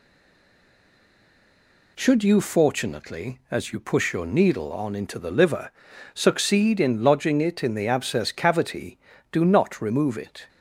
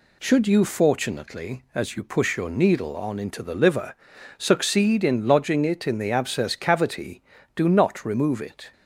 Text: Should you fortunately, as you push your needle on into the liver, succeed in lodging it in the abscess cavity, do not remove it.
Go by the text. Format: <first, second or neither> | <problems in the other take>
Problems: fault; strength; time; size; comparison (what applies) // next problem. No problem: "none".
second | stays silent before the first word; noticeable; until 1.9 s; 1.9 s long